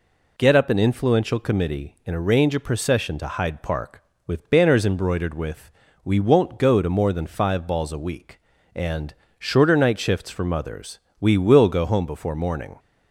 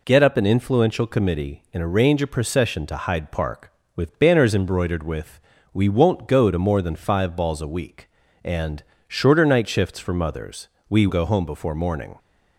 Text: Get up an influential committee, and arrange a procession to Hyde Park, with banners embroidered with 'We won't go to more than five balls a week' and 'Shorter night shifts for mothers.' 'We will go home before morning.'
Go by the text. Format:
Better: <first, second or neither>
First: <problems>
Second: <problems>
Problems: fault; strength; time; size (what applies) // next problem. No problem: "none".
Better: first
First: pauses between "with" and "We"; slight; at 5.7 s; 0.34 s long // pauses between "and" and "Shorter"; slight; at 9.1 s; 0.28 s long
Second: pauses between "with" and "We"; slight; at 5.3 s; 0.34 s long // pauses between "and" and "Shorter"; slight; at 8.8 s; 0.28 s long // skips "will"; at 11.0 s